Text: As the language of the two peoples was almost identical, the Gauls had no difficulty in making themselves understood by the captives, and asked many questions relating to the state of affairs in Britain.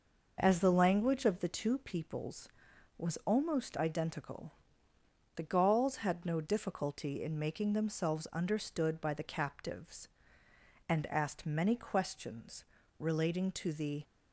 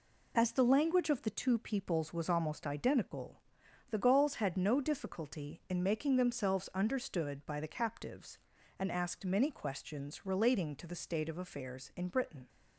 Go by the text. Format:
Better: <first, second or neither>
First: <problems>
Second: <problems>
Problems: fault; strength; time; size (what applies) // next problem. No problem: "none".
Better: second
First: pauses between "questions" and "relating"; slight; at 12.6 s; 0.36 s long // stops before "state of affairs in Britain"; at 14.0 s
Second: none